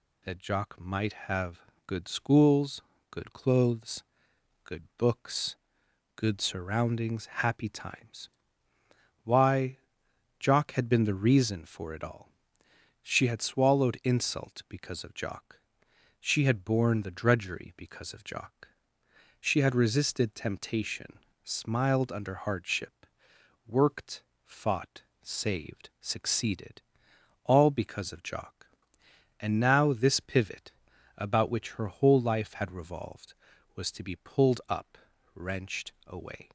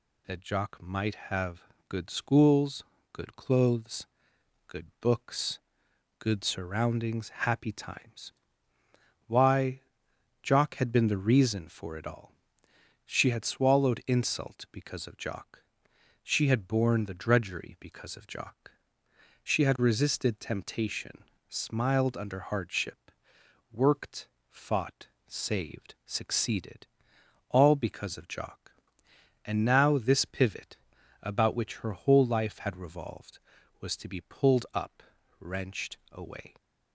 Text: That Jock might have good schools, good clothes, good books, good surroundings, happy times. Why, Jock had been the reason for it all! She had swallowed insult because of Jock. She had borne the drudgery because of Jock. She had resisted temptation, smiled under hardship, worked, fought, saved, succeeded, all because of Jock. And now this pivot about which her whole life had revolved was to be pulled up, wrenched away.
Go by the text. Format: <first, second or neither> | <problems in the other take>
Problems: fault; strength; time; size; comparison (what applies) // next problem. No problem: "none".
neither | pauses between "have" and "good"; slight; the same in both // pauses between "pivot" and "about"; noticeable; the same in both